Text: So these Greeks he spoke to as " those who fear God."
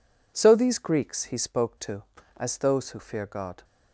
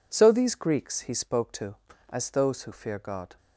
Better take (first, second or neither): neither